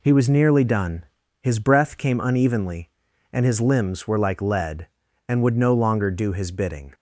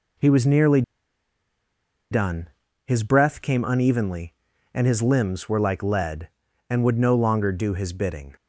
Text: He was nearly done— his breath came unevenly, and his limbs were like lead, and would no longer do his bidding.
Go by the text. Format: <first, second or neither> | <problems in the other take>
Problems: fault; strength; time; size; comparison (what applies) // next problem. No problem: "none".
first | pauses between "nearly" and "done"; strong; at 0.8 s; 1.2 s long